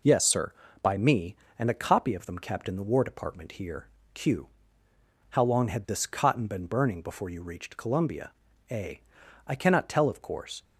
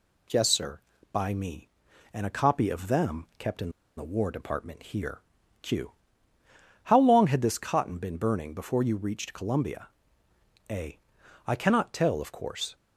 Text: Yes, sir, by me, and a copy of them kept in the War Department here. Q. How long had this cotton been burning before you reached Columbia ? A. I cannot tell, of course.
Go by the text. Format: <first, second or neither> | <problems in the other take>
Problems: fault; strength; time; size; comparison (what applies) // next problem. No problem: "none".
first | pauses between "in" and "the"; slight; at 3.6 s; 0.27 s long